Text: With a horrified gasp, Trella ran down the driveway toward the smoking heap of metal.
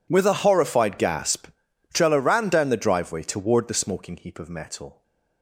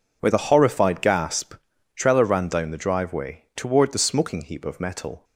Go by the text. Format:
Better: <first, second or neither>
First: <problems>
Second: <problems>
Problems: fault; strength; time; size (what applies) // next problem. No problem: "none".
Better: neither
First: none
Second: none